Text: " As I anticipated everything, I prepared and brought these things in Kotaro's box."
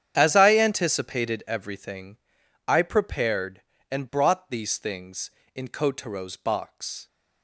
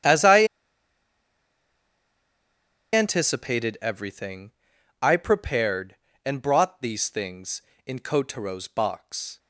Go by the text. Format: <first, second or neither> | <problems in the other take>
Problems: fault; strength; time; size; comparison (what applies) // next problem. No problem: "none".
first | starts louder than the rest; strong; until 3.5 s; 9 dB; strong in the first // pauses between "I" and "anticipated"; strong; at 0.4 s; 2.4 s long